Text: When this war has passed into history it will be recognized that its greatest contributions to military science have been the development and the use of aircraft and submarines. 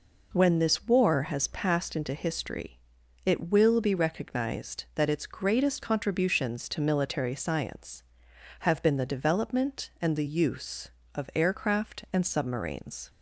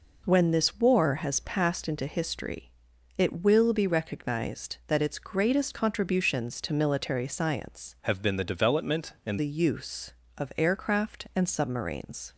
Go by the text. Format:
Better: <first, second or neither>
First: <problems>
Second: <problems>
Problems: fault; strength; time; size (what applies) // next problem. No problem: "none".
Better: first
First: pauses between "history" and "it"; noticeable; at 2.7 s; 0.46 s long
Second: pauses between "history" and "it"; noticeable; at 2.6 s; 0.46 s long // changes voice from "have" to "and"; from 8.0 to 9.3 s; 1.3 s long